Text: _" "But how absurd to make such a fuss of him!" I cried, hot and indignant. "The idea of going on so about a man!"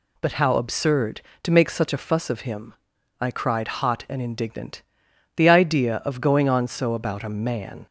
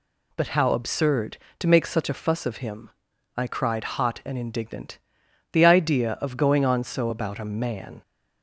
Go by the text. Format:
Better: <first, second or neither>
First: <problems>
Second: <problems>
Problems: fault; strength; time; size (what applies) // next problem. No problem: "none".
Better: neither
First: none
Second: none